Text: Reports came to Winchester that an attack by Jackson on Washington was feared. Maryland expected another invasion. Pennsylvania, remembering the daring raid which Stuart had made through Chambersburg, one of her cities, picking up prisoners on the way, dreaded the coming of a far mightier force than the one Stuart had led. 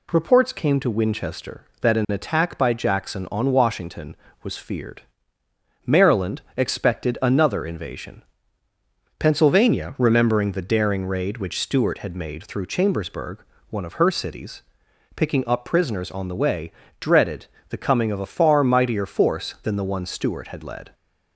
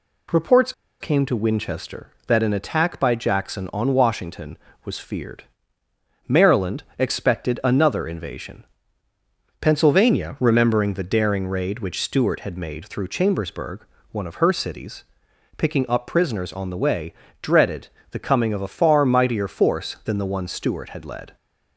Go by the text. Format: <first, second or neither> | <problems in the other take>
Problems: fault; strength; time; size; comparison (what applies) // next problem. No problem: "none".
first | pauses between "Reports" and "came"; slight; at 0.7 s; 0.29 s long // pauses between "dreaded" and "the"; slight; at 17.8 s; 0.22 s long; slight in the first